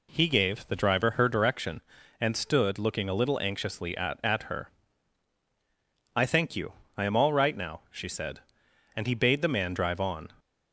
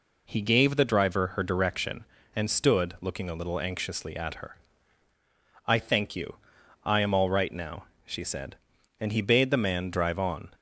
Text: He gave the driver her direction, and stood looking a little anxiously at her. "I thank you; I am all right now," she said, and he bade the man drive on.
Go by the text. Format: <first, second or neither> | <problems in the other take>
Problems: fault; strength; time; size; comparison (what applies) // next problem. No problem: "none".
second | says "at" twice; at 4.2 s